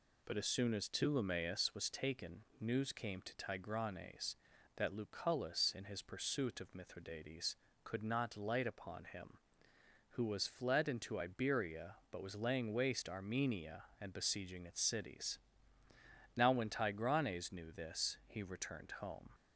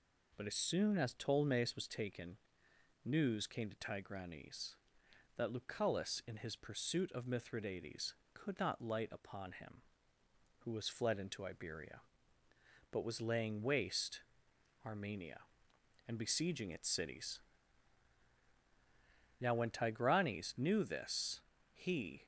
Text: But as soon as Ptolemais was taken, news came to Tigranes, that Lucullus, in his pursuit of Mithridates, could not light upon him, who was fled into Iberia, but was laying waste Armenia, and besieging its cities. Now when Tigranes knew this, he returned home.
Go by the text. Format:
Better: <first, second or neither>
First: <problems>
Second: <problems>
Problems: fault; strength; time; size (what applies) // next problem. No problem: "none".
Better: first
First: none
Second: pauses between "waste" and "Armenia"; noticeable; at 14.2 s; 0.64 s long // stops before "returned home"; at 22.2 s